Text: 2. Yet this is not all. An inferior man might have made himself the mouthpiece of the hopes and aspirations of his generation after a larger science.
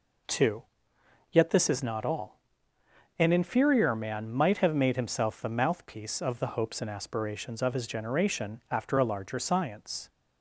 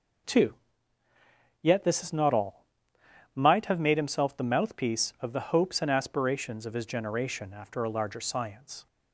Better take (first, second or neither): first